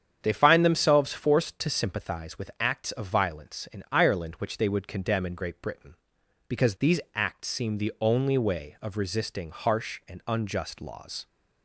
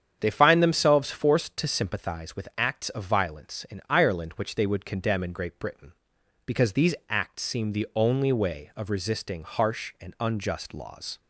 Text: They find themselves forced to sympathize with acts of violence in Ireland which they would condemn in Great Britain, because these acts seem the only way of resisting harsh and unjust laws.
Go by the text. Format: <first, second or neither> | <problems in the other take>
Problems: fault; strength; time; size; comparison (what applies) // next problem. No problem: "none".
neither | starts louder than the rest; strong; the same in both